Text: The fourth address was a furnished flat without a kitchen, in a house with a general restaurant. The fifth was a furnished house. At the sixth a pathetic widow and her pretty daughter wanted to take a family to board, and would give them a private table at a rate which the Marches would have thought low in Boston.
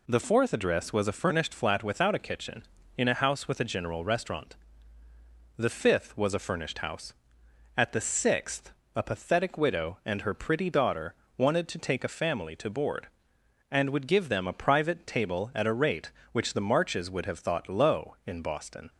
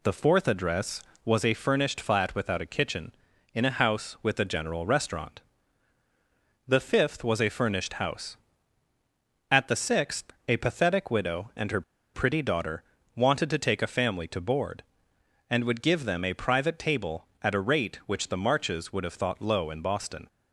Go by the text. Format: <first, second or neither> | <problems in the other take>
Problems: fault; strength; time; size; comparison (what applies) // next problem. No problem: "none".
first | pauses between "sixth" and "a"; slight; at 10.3 s; 0.16 s long; slight in the first // pauses between "her" and "pretty"; slight; at 11.8 s; 0.32 s long // pauses between "daughter" and "wanted"; slight; at 12.8 s; 0.32 s long; slight in the first